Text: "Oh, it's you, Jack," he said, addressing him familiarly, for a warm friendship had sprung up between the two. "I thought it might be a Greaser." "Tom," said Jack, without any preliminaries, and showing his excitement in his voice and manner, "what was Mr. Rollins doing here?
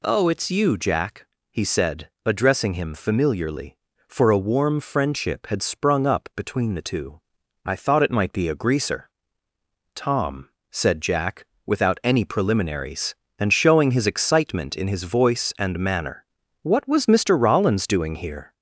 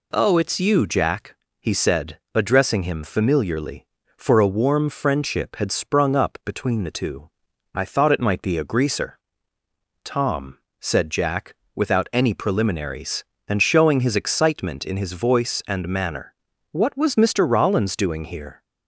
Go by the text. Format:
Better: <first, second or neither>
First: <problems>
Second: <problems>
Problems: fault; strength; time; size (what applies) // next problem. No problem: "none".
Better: second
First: gets louder; slight; throughout; 3 dB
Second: none